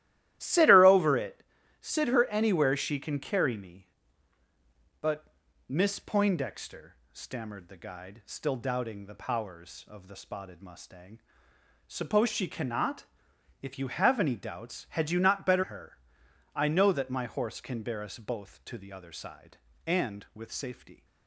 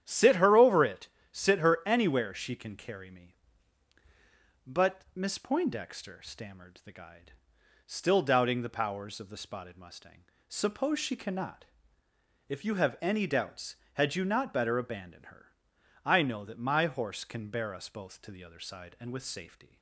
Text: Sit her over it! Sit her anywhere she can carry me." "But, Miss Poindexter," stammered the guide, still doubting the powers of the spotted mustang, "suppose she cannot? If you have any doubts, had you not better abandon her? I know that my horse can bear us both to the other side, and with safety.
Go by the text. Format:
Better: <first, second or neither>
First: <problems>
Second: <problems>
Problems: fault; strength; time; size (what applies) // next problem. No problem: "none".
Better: second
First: starts louder than the rest; strong; until 1.4 s; 14 dB // skips "abandon"; at 15.6 s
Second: starts louder than the rest; strong; until 1.0 s; 10 dB